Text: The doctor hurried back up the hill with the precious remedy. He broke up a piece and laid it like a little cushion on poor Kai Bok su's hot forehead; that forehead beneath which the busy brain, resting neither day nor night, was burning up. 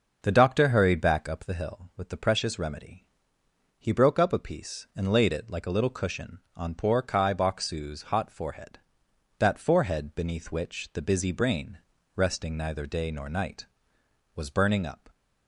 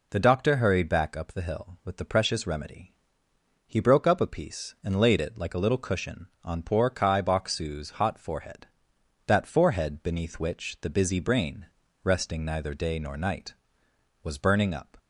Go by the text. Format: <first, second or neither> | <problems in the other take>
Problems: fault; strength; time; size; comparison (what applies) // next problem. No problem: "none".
second | starts louder than the rest; noticeable; until 1.7 s; 5.5 dB